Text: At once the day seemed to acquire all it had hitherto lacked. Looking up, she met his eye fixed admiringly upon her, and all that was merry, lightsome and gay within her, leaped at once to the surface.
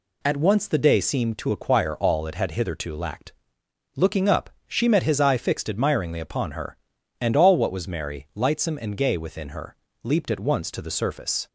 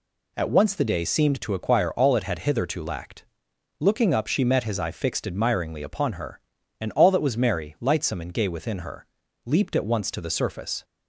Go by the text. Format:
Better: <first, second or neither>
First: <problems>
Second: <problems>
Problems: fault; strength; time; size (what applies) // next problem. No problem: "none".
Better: second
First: says "what" for "that"; at 7.5 s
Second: none